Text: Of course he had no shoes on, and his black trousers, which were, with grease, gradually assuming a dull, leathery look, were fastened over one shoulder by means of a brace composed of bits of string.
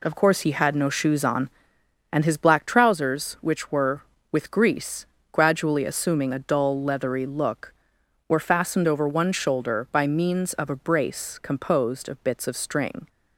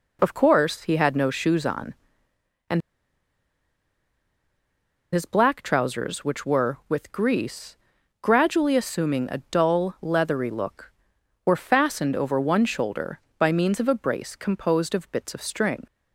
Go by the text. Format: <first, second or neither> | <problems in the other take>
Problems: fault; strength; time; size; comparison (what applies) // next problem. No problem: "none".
first | pauses between "and" and "his"; strong; at 2.8 s; 2.3 s long